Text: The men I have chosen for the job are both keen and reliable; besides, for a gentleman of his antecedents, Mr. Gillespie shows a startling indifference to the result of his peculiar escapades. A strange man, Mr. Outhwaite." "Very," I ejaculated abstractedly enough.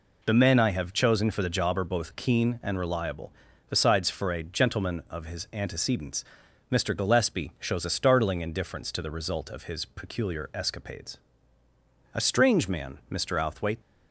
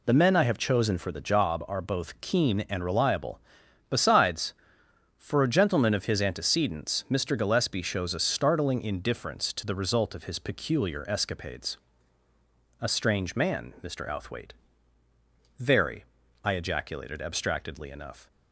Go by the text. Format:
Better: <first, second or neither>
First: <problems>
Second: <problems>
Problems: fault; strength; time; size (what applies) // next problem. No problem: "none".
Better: second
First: stops before "Very I ejaculated abstractedly enough"; at 13.7 s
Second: none